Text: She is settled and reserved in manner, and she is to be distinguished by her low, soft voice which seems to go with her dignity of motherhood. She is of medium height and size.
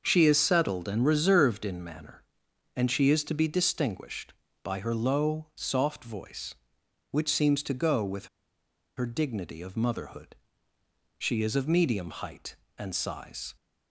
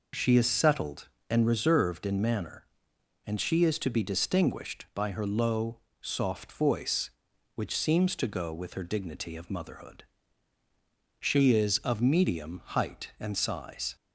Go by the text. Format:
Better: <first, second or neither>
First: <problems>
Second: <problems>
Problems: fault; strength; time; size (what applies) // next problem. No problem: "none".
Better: second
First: starts louder than the rest; until 1.0 s; 6 dB // pauses between "with" and "her"; noticeable; at 8.2 s; 0.70 s long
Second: none